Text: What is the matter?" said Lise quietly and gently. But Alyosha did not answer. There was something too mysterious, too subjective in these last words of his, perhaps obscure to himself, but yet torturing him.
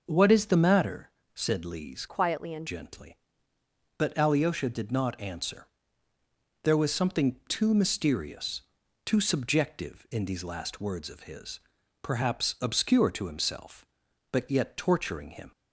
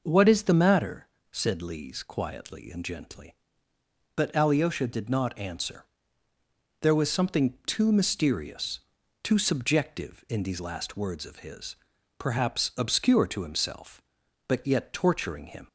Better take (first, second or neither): second